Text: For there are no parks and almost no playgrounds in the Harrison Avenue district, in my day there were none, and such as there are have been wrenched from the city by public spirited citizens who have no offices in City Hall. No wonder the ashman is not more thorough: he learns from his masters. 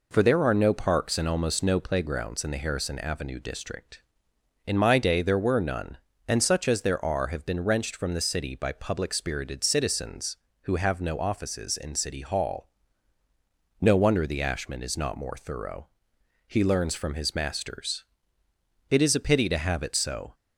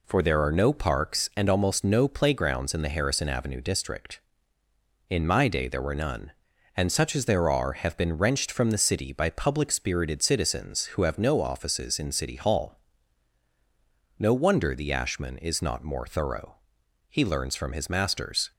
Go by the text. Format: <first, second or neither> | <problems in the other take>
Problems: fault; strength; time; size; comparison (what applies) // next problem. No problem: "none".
second | goes on to say "It is a pity to have it so"; from 18.8 s on; 1.4 s long